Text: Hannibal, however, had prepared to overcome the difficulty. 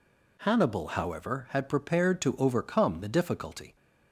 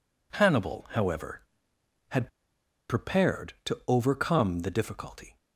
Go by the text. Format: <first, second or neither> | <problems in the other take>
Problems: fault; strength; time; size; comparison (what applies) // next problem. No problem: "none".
first | pauses between "had" and "prepared"; noticeable; at 2.2 s; 0.60 s long